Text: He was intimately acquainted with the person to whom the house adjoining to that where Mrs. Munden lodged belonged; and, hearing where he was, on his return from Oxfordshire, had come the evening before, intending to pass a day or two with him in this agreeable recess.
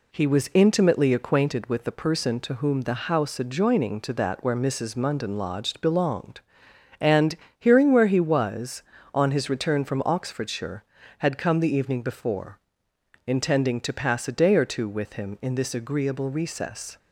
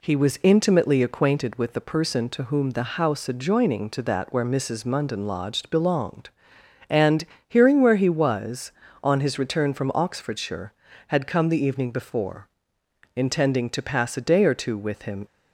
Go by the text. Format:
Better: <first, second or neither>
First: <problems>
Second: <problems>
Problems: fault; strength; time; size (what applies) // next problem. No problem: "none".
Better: first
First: none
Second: stops before "in this agreeable recess"; at 15.2 s